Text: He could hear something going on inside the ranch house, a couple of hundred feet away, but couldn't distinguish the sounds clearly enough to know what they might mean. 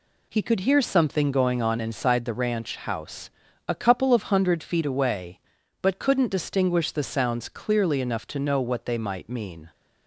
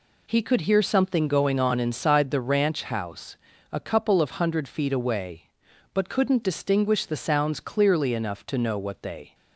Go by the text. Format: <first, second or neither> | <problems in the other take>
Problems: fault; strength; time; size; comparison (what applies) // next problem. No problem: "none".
first | stops before "might mean"; at 9.3 s